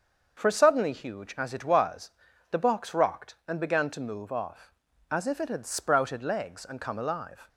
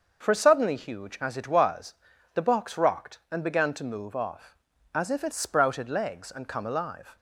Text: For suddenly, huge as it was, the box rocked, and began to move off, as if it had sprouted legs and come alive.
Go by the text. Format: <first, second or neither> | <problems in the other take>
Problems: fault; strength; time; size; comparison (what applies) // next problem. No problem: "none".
first | starts louder than the rest; noticeable; until 1.2 s; 6 dB; also in the first // skips "had"; at 5.3 s